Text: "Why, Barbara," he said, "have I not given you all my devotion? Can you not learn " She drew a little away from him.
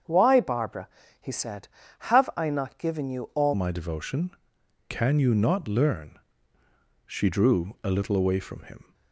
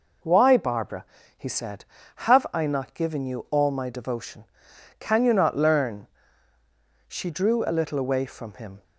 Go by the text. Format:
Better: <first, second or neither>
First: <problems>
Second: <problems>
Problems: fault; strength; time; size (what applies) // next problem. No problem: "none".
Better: second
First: starts louder than the rest; strong; until 1.3 s; 7.5 dB // changes voice at "my"; from 3.5 s on; 5.4 s long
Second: none